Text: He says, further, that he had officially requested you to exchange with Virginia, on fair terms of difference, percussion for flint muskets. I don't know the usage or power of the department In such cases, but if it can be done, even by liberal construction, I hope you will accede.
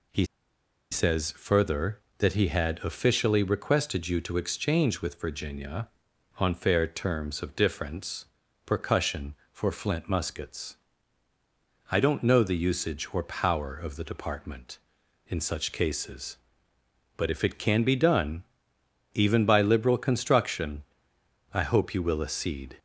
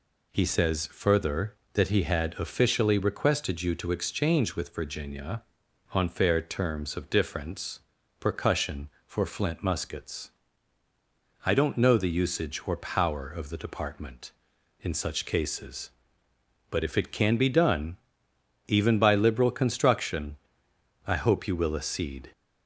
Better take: second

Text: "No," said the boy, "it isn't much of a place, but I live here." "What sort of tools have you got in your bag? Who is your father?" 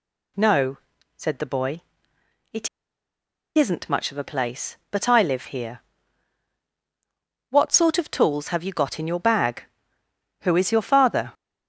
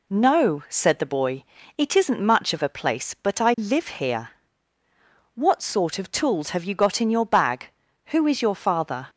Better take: second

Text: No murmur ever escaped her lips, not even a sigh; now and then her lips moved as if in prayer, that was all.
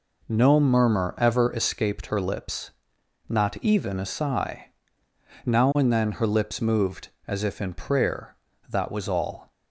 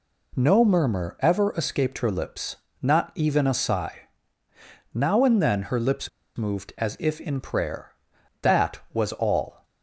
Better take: first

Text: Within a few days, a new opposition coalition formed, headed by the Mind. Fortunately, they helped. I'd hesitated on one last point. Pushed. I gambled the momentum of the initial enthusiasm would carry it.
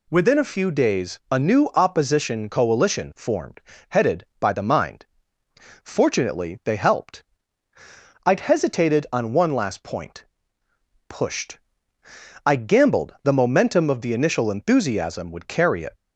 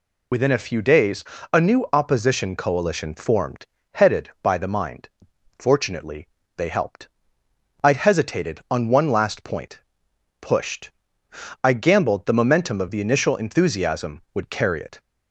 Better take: first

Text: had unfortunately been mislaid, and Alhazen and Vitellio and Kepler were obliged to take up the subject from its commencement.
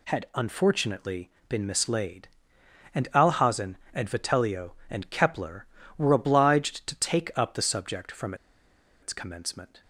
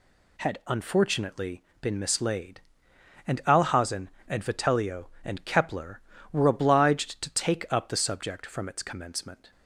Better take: second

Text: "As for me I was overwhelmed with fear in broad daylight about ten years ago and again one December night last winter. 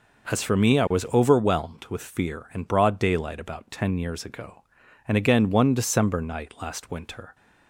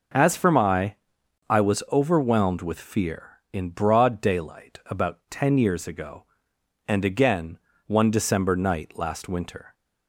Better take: first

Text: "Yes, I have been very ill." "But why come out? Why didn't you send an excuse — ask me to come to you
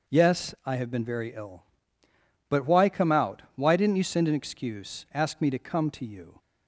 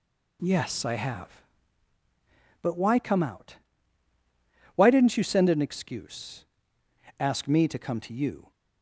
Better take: first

